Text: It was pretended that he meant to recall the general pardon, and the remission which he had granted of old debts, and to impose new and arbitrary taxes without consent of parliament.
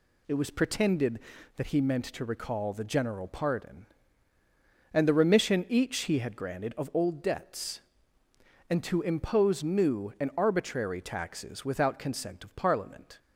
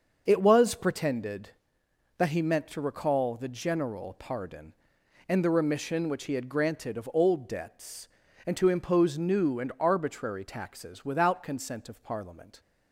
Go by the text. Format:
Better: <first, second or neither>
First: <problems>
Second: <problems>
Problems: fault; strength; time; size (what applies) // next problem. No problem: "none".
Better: second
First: says "each" for "which"; at 5.6 s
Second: none